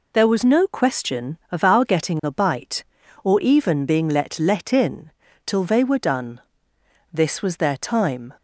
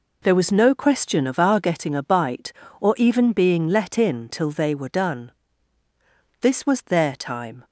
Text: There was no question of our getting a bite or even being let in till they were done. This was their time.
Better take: second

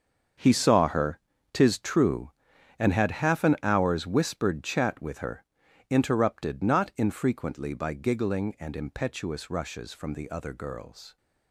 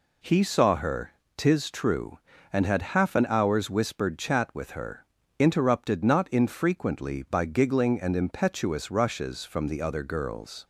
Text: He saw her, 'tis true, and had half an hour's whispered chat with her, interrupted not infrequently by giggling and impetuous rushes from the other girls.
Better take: second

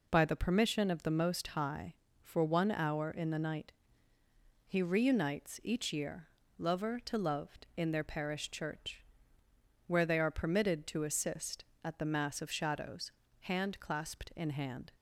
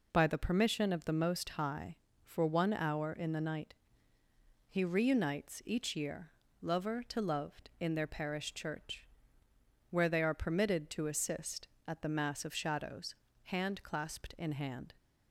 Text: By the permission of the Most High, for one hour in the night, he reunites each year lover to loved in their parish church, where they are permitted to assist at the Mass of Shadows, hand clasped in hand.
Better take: neither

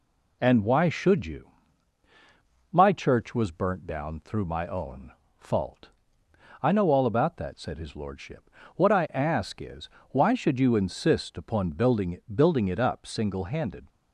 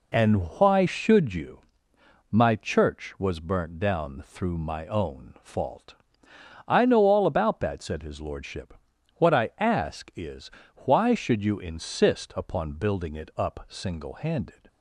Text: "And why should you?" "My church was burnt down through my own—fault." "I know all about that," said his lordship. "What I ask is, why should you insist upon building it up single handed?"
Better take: second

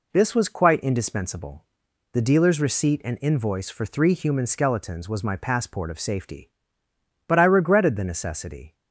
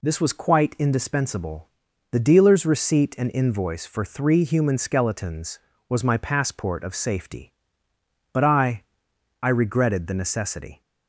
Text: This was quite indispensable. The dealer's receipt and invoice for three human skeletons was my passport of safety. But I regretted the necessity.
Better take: first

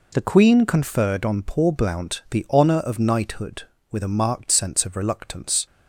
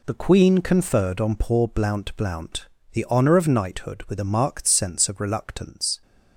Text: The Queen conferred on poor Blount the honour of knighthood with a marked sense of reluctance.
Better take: first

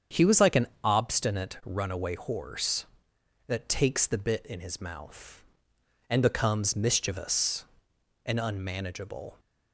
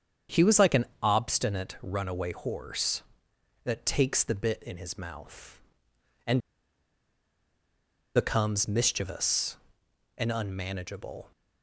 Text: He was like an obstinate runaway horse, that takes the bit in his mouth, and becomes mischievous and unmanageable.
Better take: first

